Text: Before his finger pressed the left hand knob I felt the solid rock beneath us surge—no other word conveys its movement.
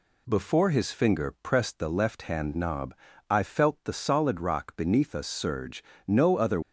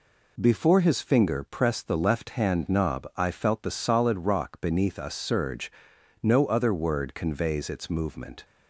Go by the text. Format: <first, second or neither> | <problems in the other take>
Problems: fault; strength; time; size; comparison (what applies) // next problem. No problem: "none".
second | pauses between "knob" and "I"; slight; at 2.9 s; 0.34 s long // stops before "word conveys its movement"; at 6.6 s